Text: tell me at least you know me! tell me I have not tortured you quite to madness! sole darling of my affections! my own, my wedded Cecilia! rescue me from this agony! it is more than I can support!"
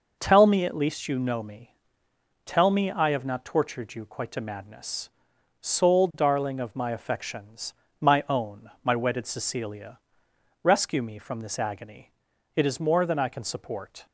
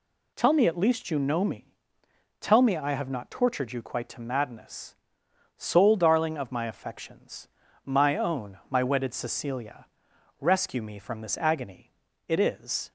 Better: first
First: none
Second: stops before "more than I can support"; at 12.8 s

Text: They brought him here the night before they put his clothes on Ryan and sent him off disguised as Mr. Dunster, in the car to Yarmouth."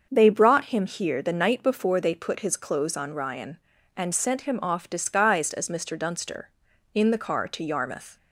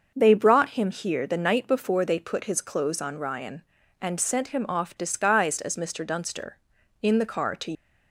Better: first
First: starts louder than the rest; until 1.1 s; 6.5 dB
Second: starts louder than the rest; until 1.1 s; 6 dB // stops before "Yarmouth"; at 7.7 s

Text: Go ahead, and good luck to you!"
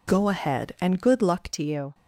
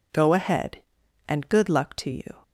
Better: second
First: changes voice at "to"; from 1.5 s on; 0.4 s long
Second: none

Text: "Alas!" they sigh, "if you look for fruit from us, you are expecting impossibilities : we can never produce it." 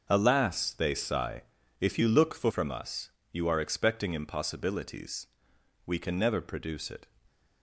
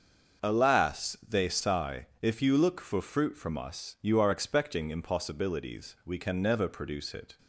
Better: second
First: starts louder than the rest; noticeable; until 1.1 s; 6 dB // skips "fruit"; at 2.4 s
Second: starts louder than the rest; until 1.5 s; 6.5 dB

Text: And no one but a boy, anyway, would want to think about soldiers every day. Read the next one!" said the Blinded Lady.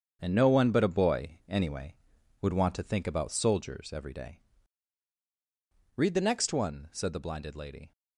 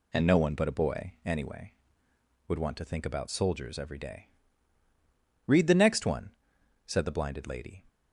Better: second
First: gets quieter; strong; throughout; 10 dB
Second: none

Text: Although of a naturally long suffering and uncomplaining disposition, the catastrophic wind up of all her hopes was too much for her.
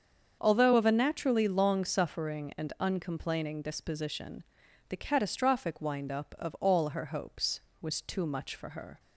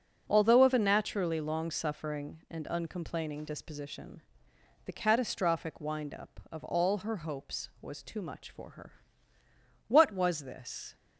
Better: first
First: starts louder than the rest; until 1.4 s; 7 dB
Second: starts louder than the rest; noticeable; until 1.2 s; 6 dB // goes on to say "What was this"; noticeable; from 9.8 s on; 1.0 s long

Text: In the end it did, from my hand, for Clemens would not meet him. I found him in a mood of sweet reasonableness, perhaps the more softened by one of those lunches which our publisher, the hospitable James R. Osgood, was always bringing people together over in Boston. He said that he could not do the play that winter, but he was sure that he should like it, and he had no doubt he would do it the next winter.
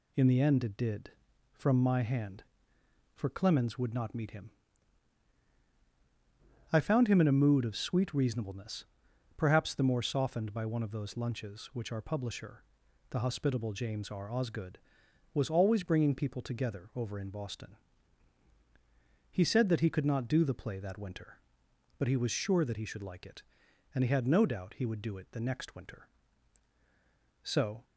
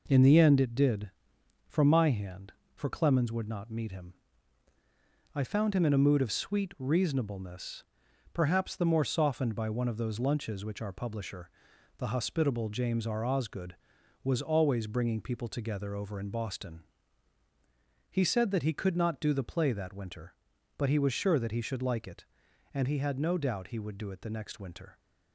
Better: second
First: goes on to say "So"; slight; from 27.4 s on; 0.40 s long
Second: none

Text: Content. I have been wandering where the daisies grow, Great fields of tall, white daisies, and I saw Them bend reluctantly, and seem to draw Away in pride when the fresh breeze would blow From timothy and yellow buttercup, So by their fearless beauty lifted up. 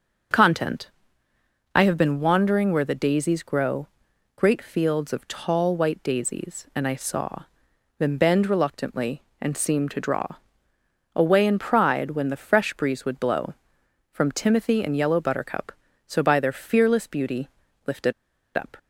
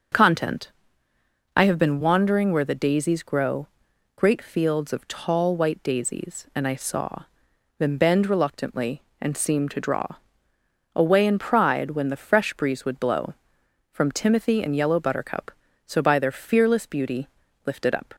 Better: second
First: pauses between "saw" and "Them"; noticeable; at 7.4 s; 0.54 s long // pauses between "draw" and "Away"; noticeable; at 10.2 s; 0.88 s long // pauses between "beauty" and "lifted"; slight; at 17.4 s; 0.36 s long // pauses between "lifted" and "up"; at 18.1 s; 0.44 s long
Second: pauses between "saw" and "Them"; noticeable; at 7.2 s; 0.54 s long // pauses between "draw" and "Away"; noticeable; at 10.0 s; 0.88 s long // pauses between "beauty" and "lifted"; slight; at 17.2 s; 0.36 s long

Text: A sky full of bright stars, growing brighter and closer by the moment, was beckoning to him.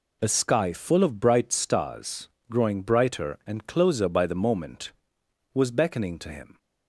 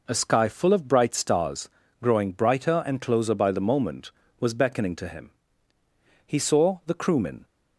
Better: first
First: none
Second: goes on to say "He saw the Crewmen"; noticeable; from 6.2 s on; 1.1 s long

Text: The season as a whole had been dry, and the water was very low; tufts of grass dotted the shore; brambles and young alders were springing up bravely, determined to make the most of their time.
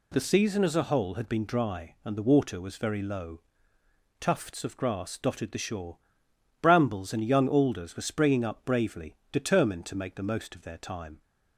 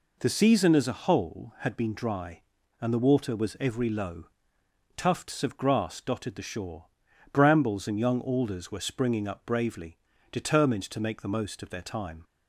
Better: first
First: none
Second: says "every" for "very"; at 3.5 s

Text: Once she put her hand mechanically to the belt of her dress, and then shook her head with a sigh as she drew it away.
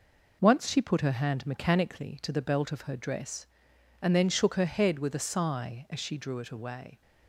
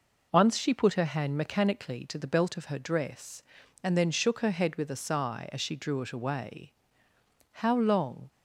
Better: first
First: none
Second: goes on to say "How long"; noticeable; from 7.5 s on; 0.78 s long

